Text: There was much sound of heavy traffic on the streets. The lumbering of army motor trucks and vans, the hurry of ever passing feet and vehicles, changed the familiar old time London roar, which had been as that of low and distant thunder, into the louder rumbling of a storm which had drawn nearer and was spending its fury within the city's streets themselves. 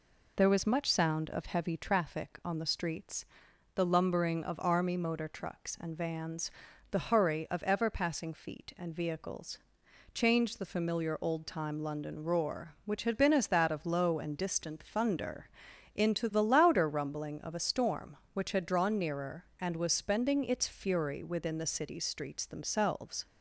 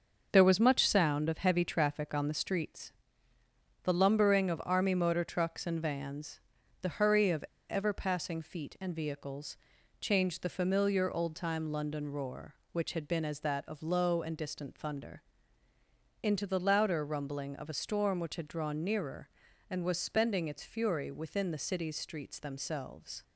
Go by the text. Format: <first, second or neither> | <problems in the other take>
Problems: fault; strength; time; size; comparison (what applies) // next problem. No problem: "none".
first | starts louder than the rest; until 1.3 s; 6 dB // pauses between "of" and "ever"; slight; at 7.4 s; 0.27 s long